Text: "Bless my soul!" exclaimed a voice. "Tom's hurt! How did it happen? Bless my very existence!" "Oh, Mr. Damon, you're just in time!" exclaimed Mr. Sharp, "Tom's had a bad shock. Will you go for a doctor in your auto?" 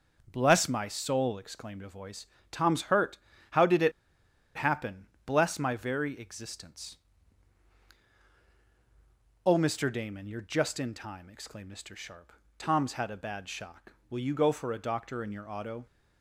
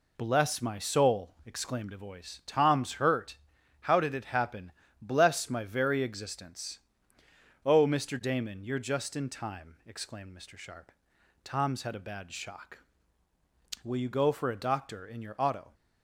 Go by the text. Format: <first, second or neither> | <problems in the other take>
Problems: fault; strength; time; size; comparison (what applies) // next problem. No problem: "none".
second | pauses between "it" and "happen"; noticeable; at 3.9 s; 0.65 s long